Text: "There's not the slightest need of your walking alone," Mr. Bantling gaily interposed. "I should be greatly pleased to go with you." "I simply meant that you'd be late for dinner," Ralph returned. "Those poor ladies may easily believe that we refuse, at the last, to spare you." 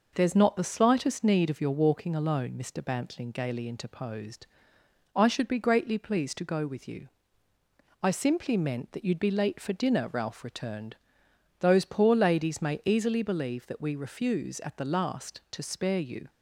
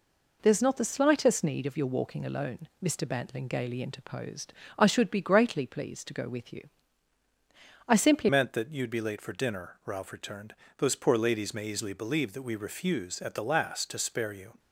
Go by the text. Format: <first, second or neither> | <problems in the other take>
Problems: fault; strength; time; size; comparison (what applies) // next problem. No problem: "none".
first | changes voice at "meant"; from 8.2 s on; 6.3 s long